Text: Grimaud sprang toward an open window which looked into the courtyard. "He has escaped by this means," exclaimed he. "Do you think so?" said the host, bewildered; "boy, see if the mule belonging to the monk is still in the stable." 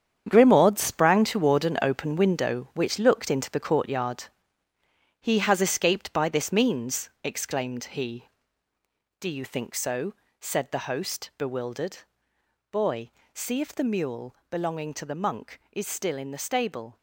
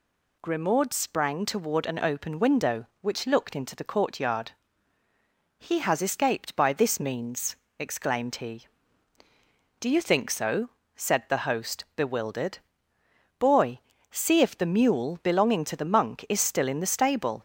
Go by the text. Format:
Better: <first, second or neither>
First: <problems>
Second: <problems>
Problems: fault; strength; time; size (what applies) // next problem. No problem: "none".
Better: second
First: gets quieter; strong; throughout; 11 dB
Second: none